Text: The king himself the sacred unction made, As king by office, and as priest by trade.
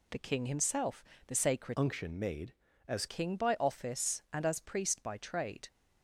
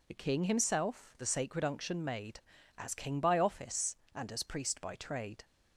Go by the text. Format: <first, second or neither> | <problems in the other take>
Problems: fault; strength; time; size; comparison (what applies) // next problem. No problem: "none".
second | pauses between "himself" and "the"; slight; at 1.0 s; 0.24 s long // changes voice from "unction" to "As"; from 1.7 to 3.0 s; 1.3 s long